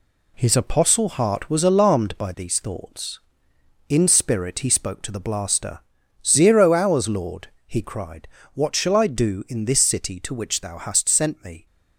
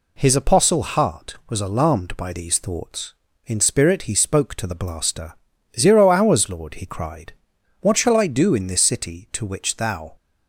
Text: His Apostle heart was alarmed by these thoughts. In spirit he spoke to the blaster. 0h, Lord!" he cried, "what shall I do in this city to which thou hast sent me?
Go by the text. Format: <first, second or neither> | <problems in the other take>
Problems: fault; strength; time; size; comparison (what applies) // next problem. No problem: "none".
first | stops before "hast sent me"; at 10.1 s